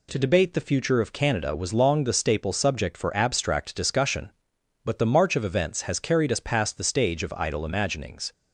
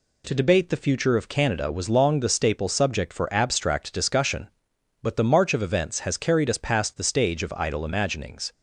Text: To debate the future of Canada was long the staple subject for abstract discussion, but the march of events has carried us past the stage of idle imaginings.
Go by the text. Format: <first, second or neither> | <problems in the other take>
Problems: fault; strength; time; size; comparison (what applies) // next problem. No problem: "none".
neither | none